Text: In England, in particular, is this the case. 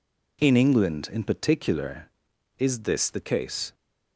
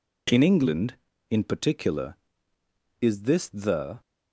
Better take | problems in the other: first | stops before "case"; at 4.0 s

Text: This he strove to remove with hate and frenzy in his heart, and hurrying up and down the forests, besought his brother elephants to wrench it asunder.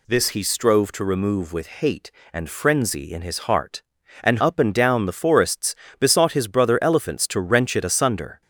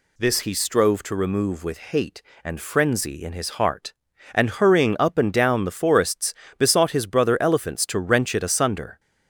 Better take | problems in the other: second | skips "hurrying"; at 4.3 s

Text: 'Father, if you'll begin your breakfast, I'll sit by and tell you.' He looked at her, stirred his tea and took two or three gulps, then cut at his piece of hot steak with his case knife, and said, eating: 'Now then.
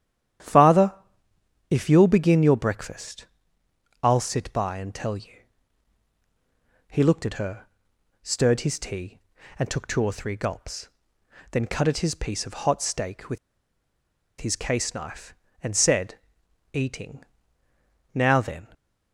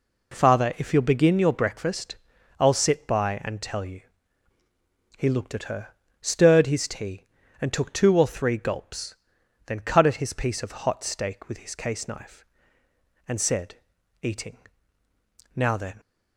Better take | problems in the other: second | starts louder than the rest; strong; until 2.1 s; 10.5 dB // pauses between "with" and "his"; at 13.3 s; 1.0 s long

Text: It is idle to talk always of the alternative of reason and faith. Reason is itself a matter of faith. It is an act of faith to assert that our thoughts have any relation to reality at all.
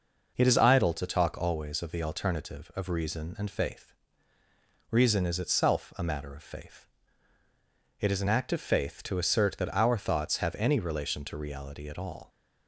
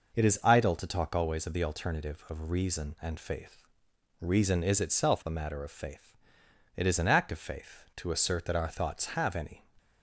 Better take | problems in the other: first | stops before "relation to reality at all"; at 9.7 s

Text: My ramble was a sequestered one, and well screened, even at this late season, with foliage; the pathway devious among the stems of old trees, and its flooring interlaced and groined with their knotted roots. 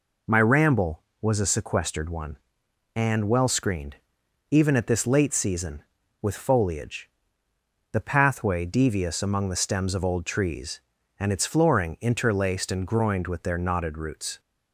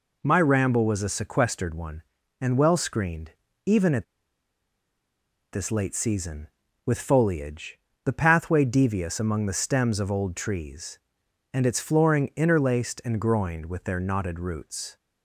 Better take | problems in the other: first | pauses between "at" and "this"; strong; at 4.0 s; 1.4 s long

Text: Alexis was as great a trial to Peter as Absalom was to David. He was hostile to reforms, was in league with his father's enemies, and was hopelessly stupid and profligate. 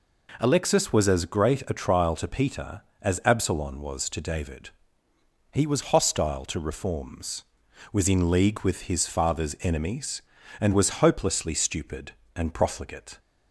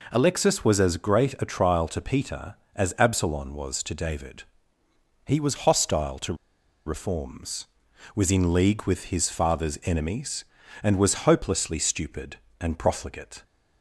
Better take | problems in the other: first | pauses between "to" and "reforms"; noticeable; at 6.3 s; 0.52 s long

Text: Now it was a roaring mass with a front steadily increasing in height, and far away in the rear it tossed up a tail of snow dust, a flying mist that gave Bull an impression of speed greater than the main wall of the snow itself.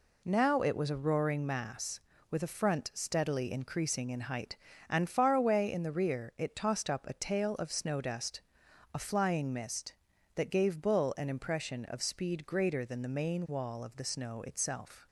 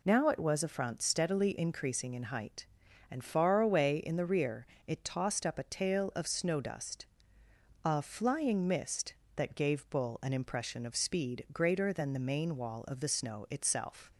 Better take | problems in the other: first | skips "a roaring mass with"; at 0.6 s // pauses between "rear" and "it"; slight; at 4.6 s; 0.20 s long

